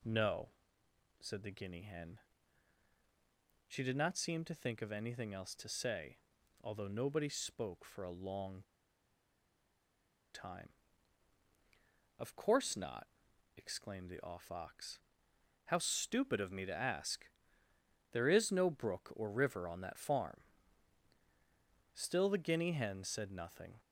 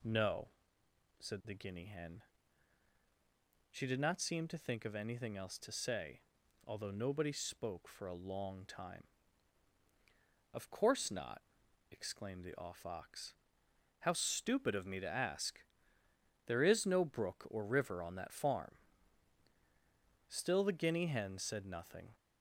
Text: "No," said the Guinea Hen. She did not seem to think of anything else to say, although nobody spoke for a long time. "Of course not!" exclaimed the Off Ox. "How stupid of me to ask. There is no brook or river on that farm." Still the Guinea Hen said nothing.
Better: second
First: pauses between "long" and "time"; strong; at 8.6 s; 1.7 s long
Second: none

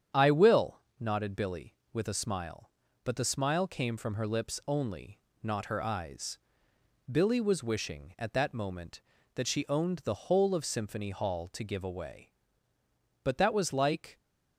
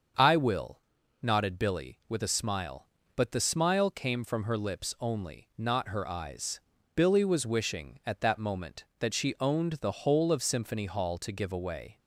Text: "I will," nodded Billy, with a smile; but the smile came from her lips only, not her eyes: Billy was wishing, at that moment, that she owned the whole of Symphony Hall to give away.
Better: second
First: starts louder than the rest; strong; until 1.3 s; 8.5 dB // goes on to say "But that was like"; noticeable; from 13.2 s on; 0.94 s long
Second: starts louder than the rest; until 1.6 s; 6.5 dB

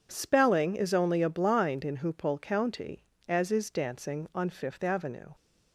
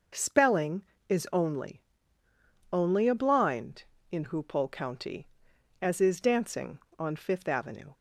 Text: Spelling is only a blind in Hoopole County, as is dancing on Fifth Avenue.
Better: first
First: none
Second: says "only" twice; at 2.7 s

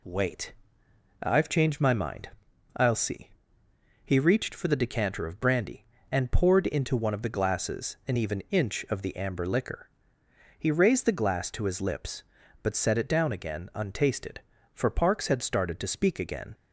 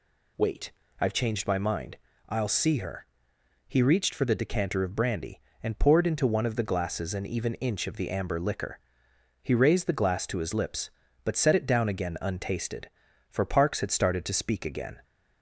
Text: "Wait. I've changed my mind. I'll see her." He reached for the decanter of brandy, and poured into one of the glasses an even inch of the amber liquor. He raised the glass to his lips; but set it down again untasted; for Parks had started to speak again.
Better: second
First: skips "her"; at 3.6 s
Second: none

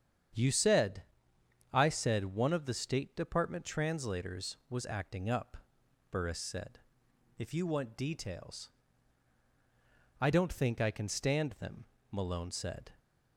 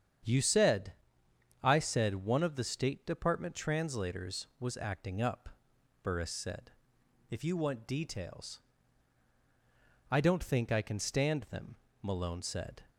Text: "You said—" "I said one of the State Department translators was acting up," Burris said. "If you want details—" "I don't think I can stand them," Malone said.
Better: neither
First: starts louder than the rest; strong; until 2.0 s; 8 dB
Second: starts louder than the rest; strong; until 1.9 s; 8 dB

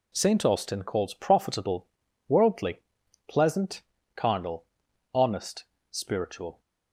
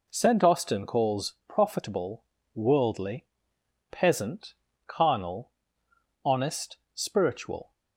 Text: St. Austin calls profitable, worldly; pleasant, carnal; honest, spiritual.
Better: first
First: none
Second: says "peasant" for "pleasant"; at 3.9 s

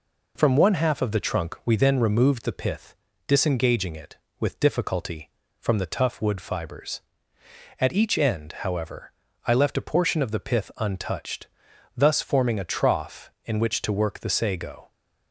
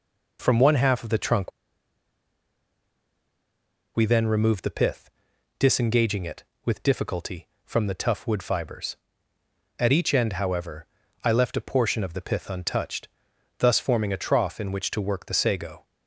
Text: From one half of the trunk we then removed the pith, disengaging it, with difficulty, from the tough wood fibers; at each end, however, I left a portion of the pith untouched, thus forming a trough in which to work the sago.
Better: first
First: none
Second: pauses between "trunk" and "we"; strong; at 1.5 s; 2.4 s long

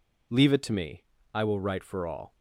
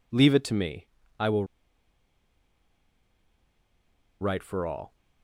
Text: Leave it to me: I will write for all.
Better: first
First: none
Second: pauses between "will" and "write"; strong; at 1.4 s; 2.7 s long

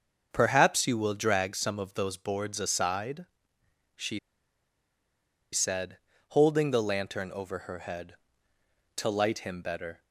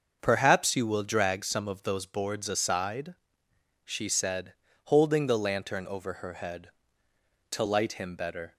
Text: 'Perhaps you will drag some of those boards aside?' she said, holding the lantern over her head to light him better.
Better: second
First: starts louder than the rest; until 1.3 s; 6.5 dB // pauses between "she" and "said"; strong; at 4.1 s; 1.3 s long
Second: starts louder than the rest; until 1.2 s; 6.5 dB

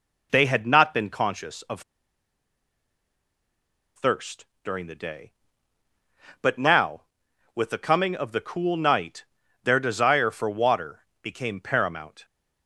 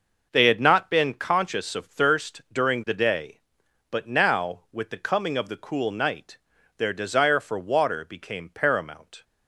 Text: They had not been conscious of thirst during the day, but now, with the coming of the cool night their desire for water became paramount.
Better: second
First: pauses between "of" and "thirst"; strong; at 1.8 s; 2.1 s long // pauses between "thirst" and "during"; slight; at 4.4 s; 0.20 s long // pauses between "night" and "their"; at 9.2 s; 0.40 s long // pauses between "water" and "became"; slight; at 11.0 s; 0.20 s long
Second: pauses between "night" and "their"; at 6.3 s; 0.40 s long

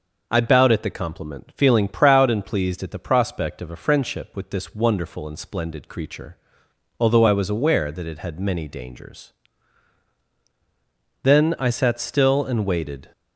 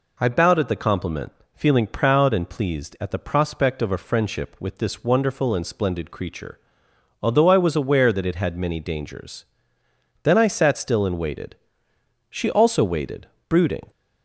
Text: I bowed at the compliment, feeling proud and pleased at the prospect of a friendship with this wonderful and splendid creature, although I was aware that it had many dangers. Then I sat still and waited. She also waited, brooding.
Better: second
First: stops before "She also waited brooding"; at 13.1 s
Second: none

